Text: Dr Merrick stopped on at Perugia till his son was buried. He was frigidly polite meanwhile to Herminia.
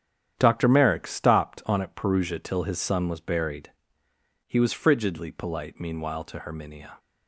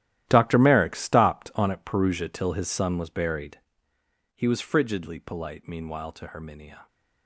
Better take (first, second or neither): first